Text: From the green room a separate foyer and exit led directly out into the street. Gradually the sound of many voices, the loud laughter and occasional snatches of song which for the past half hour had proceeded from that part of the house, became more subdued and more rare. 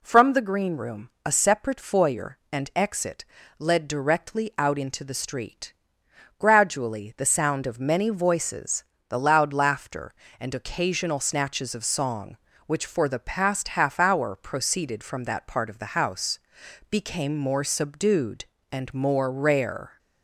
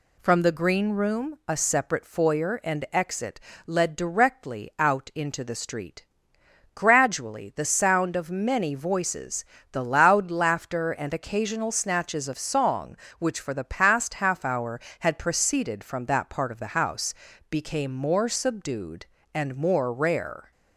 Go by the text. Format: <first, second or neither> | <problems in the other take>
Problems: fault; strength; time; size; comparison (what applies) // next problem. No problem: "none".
second | pauses between "room" and "a"; slight; at 1.1 s; 0.16 s long // pauses between "exit" and "led"; slight; at 3.2 s; 0.34 s long; slight in the second // skips "had"; at 14.3 s